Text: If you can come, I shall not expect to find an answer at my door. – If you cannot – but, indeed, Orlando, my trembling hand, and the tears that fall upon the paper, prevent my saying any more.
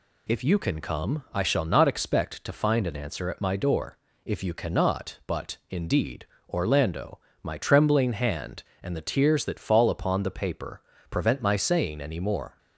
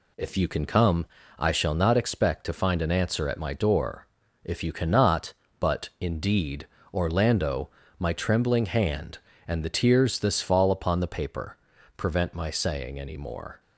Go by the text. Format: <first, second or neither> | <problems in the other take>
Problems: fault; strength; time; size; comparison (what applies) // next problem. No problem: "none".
first | says "this" for "that"; at 10.1 s